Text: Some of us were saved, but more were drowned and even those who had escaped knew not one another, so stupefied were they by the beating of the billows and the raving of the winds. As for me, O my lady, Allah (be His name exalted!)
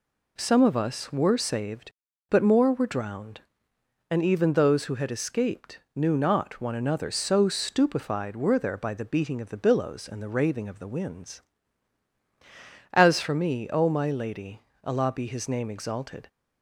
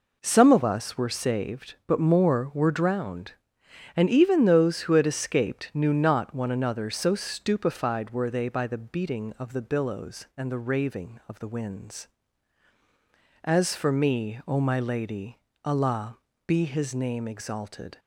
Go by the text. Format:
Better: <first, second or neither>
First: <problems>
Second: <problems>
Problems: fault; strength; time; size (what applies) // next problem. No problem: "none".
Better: second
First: pauses between "escaped" and "knew"; slight; at 5.7 s; 0.16 s long // says "there" for "they"; at 8.5 s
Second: none